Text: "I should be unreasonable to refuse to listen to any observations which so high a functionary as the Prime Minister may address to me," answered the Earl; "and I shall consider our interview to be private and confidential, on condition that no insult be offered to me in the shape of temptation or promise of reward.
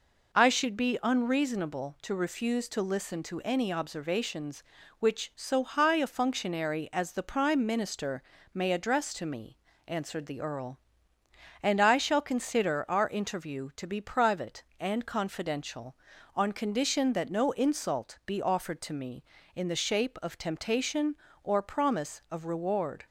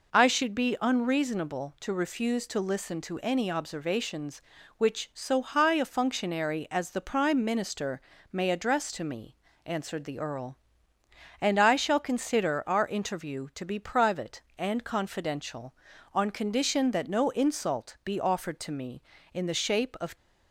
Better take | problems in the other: first | pauses between "Minister" and "may"; slight; at 8.0 s; 0.32 s long; slight in the first // stops before "temptation or promise of reward"; at 20.1 s

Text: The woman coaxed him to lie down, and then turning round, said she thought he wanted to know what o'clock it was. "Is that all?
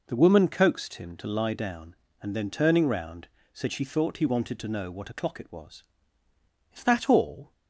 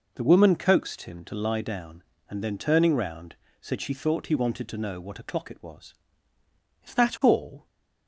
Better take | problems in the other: neither | none

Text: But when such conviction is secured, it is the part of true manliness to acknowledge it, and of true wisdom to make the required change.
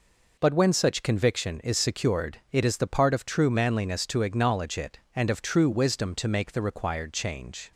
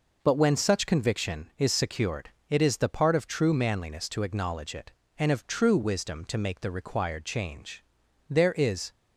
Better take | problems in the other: first | goes on to say "There is"; noticeable; from 8.2 s on; 0.62 s long

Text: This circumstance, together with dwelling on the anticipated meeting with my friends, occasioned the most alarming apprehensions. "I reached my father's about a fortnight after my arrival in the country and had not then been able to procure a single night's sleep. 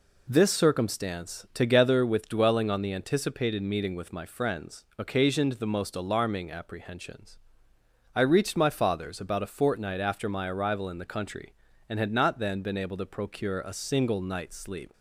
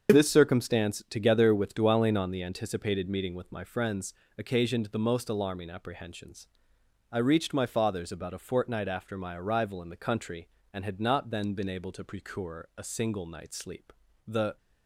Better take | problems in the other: first | starts louder than the rest; until 1.1 s; 6.5 dB // goes on to say "The"; slight; from 14.2 s on; 0.30 s long

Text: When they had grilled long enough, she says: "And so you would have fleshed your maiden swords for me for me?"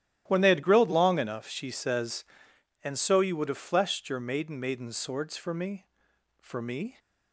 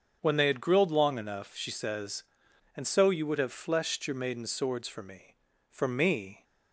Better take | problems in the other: second | starts louder than the rest; strong; until 1.2 s; 12.5 dB; also in the second // says "maiden" twice; at 4.5 s

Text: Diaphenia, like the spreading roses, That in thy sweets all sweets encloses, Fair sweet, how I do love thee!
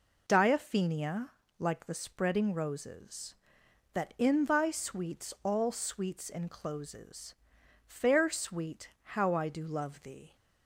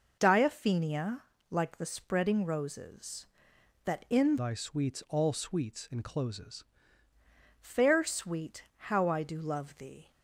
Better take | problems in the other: first | changes voice from "thy" to "encloses"; from 4.3 to 6.6 s; 2.3 s long

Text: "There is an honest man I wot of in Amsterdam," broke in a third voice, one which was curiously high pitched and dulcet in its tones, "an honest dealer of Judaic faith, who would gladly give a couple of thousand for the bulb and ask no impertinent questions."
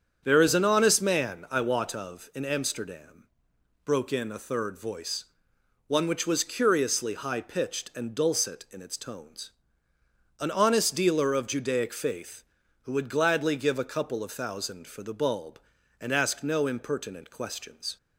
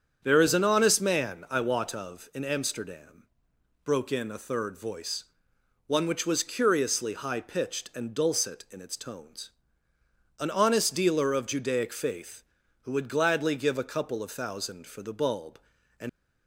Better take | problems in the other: first | starts louder than the rest; strong; until 1.2 s; 8 dB; strong in the first // stops before "ask no impertinent questions"; at 16.0 s

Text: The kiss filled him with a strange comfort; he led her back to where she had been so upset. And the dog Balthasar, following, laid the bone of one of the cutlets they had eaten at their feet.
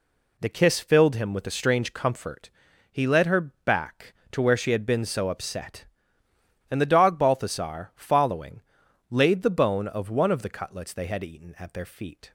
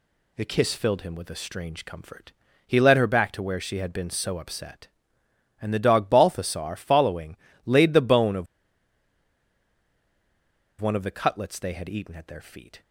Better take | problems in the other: first | pauses between "of" and "one"; strong; at 8.4 s; 2.3 s long

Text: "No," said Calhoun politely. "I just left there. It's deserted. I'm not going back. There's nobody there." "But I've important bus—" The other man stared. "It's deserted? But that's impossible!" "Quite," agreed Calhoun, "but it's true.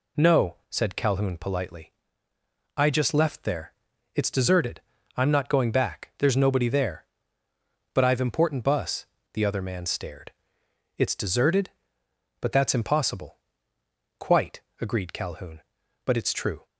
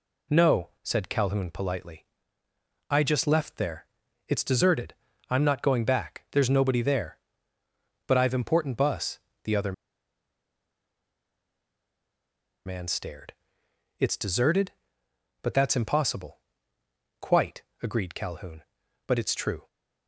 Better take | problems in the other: first | pauses between "other" and "man"; strong; at 9.7 s; 2.9 s long

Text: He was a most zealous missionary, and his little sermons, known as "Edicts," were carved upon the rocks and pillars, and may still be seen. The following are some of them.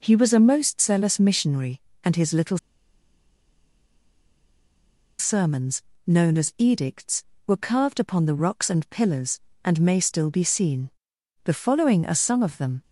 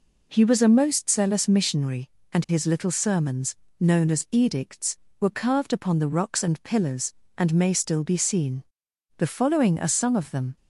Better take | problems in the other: second | pauses between "little" and "sermons"; strong; at 2.5 s; 2.6 s long

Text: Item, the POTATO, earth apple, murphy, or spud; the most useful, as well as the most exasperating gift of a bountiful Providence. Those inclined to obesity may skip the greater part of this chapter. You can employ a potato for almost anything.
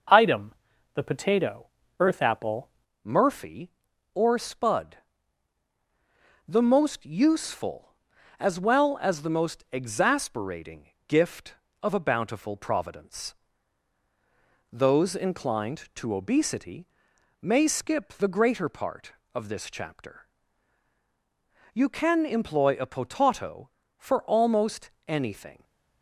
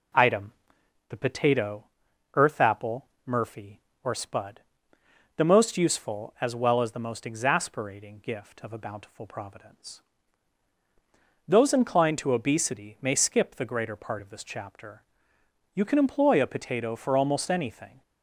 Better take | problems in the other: second | changes voice at "murphy"; from 3.0 s on; 22.6 s long // pauses between "exasperating" and "gift"; slight; at 10.8 s; 0.18 s long // pauses between "obesity" and "may"; noticeable; at 16.8 s; 0.54 s long // pauses between "almost" and "anything"; slight; at 24.8 s; 0.18 s long

